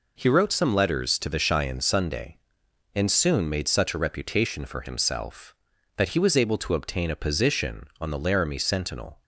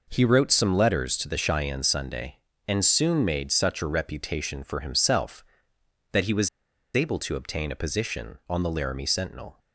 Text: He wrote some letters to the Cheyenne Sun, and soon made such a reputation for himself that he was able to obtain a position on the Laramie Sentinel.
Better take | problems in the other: first | pauses between "was" and "able"; at 6.4 s; 0.45 s long

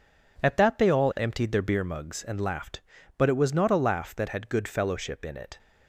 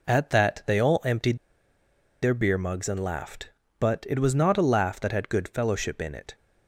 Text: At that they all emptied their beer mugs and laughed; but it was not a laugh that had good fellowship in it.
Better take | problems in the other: first | pauses between "emptied" and "their"; noticeable; at 1.3 s; 0.84 s long

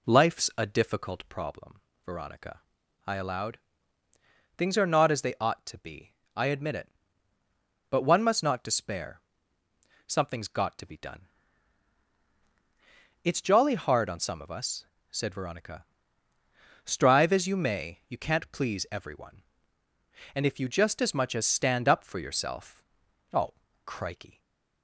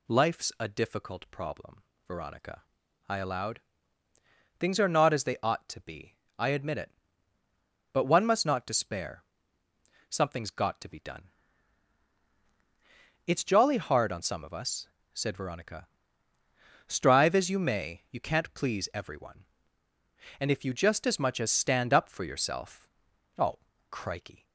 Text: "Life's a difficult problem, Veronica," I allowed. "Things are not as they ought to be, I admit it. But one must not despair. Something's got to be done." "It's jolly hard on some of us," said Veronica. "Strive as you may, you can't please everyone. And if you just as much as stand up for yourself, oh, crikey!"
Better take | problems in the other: second | starts louder than the rest; slight; until 1.5 s; 2 dB // stays silent after the last word; slight; from 24.3 s on; 0.5 s long

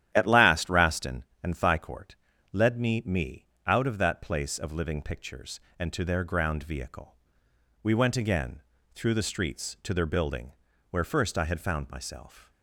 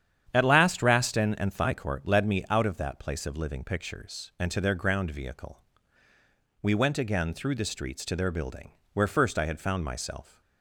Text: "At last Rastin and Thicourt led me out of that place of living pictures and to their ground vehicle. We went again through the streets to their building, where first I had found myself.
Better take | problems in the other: second | starts louder than the rest; strong; until 1.1 s; 11 dB; strong in the second // pauses between "Thicourt" and "led"; slight; at 2.1 s; 0.36 s long // says "me" twice; at 3.0 s // pauses between "again" and "through"; slight; at 8.5 s; 0.34 s long

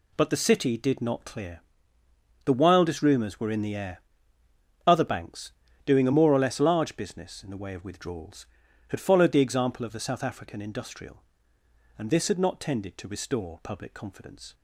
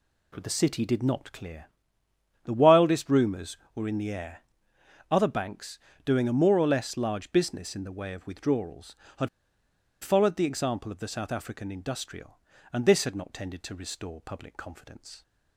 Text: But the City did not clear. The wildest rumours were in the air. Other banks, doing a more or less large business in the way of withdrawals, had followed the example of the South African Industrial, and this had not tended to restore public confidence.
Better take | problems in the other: first | pauses between "had" and "followed"; noticeable; at 9.2 s; 0.73 s long

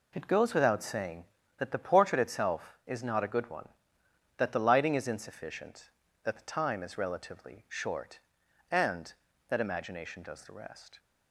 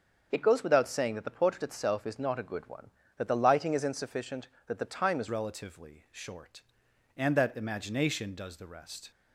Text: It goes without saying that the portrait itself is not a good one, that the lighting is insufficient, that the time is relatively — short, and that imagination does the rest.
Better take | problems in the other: first | starts louder than the rest; until 1.3 s; 6.5 dB // changes voice at "relatively"; from 5.2 s on; 3.9 s long

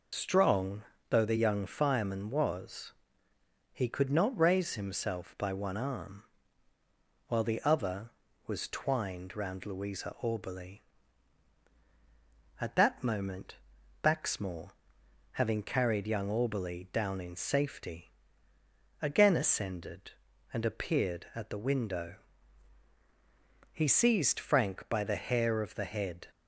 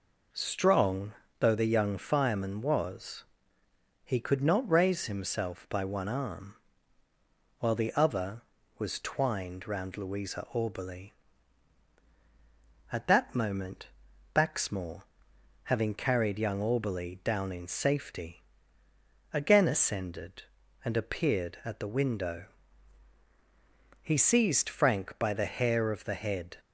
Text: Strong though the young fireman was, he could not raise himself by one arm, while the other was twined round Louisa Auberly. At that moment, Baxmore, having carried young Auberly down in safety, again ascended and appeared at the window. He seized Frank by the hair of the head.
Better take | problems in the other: second | loses the start of "Strong"; at 0.1 s; 100 ms // pauses between "Strong" and "though"; slight; at 0.8 s; 0.28 s long; slight in the second

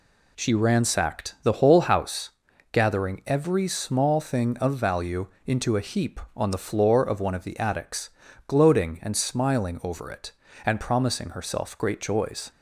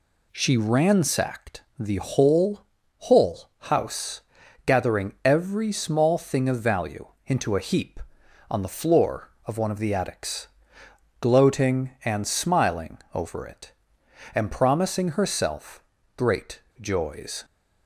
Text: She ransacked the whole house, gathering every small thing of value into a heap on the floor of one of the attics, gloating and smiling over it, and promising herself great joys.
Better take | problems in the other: first | says "whole" twice; at 3.0 s // pauses between "value" and "into"; slight; at 7.0 s; 0.18 s long; slight in the first // pauses between "smiling" and "over"; slight; at 12.9 s; 0.16 s long // pauses between "herself" and "great"; slight; at 15.8 s; 0.34 s long // pauses between "great" and "joys"; slight; at 16.6 s; 0.19 s long

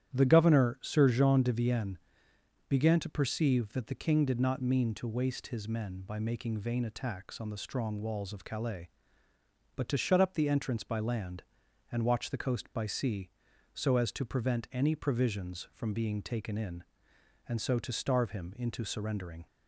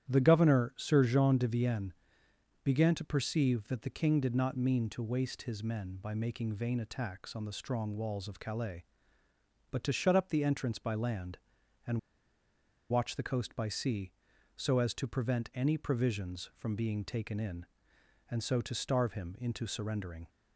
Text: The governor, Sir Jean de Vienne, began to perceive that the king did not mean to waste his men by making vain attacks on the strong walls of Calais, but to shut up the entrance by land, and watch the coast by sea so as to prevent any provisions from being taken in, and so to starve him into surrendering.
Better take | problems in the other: first | starts louder than the rest; strong; until 1.1 s; 10.5 dB; strong in the first // pauses between "and" and "watch"; noticeable; at 11.9 s; 0.92 s long

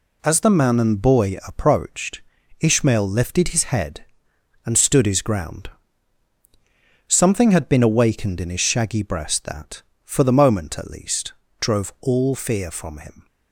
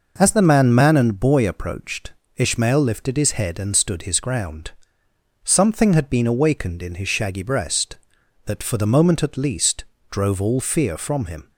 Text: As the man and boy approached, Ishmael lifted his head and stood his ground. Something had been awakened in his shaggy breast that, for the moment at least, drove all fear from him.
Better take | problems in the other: first | says "man" twice; at 0.7 s

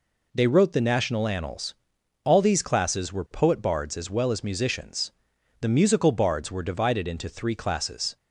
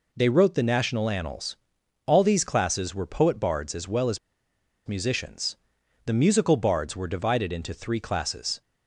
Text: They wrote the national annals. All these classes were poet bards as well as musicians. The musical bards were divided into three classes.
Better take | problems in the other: first | pauses between "as" and "musicians"; noticeable; at 4.1 s; 0.68 s long

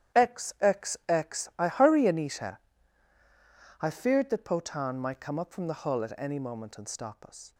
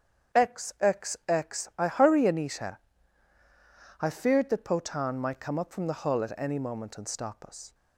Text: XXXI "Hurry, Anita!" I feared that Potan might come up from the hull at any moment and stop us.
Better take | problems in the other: second | gets quieter; strong; throughout; 12.5 dB // starts louder than the rest; strong; until 1.3 s; 10.5 dB; strong in the second

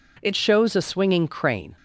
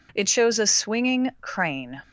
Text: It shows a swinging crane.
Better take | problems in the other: second | changes voice at "shows"; from 0.3 s on; 1.4 s long

